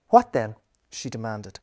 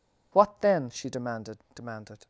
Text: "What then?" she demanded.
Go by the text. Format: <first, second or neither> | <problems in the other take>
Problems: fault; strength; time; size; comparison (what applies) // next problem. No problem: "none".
first | says "demanded" twice; at 1.7 s